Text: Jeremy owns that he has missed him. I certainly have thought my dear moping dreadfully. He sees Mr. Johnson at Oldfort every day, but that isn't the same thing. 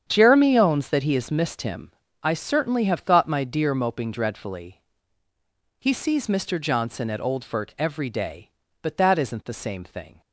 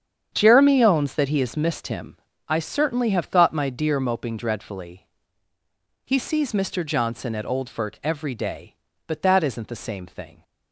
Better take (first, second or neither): neither